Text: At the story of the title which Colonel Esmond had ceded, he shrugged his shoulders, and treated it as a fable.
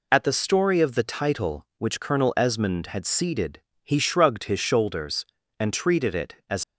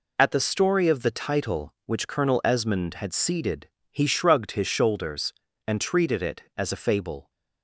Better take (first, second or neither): second